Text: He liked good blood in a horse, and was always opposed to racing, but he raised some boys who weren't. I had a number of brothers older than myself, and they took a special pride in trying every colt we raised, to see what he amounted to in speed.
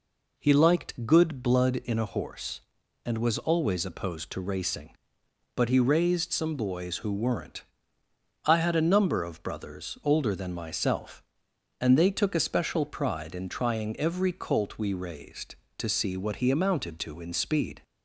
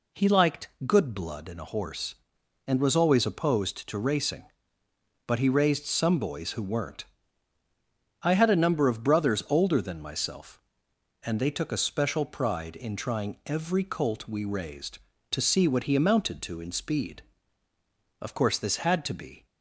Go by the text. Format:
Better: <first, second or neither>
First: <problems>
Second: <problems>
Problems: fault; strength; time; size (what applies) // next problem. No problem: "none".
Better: first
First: none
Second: pauses between "liked" and "good"; slight; at 0.6 s; 0.18 s long // goes on to say "Of course this had to be"; noticeable; from 18.2 s on; 1.2 s long